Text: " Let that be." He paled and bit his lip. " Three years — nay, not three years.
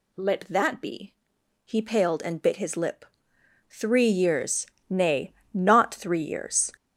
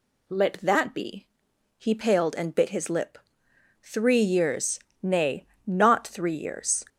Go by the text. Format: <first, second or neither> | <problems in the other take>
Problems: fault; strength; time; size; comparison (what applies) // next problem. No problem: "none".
second | gets louder; strong; throughout; 8.5 dB